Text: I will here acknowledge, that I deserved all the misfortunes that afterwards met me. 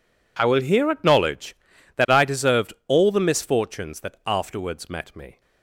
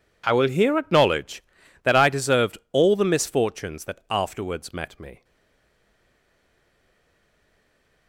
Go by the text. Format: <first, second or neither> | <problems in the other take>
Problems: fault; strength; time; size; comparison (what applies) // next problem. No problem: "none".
first | pauses between "deserved" and "all"; slight; at 2.5 s; 0.16 s long; slight in the first // stays silent after the last word; strong; from 5.2 s on; 2.8 s long